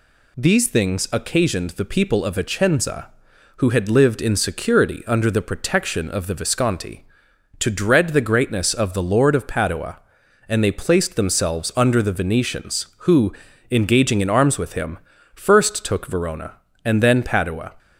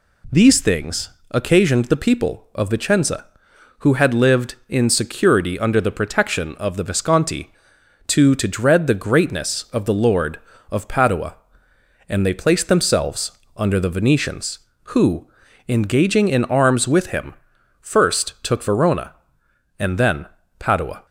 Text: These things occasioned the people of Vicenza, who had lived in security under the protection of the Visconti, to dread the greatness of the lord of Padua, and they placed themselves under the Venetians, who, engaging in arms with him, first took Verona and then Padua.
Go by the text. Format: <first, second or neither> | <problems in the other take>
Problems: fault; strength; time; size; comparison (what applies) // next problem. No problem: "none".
first | pauses between "things" and "occasioned"; slight; at 1.0 s; 0.22 s long // says "to" twice; at 8.3 s // pauses between "themselves" and "under"; slight; at 13.3 s; 0.24 s long // pauses between "then" and "Padua"; slight; at 20.2 s; 0.34 s long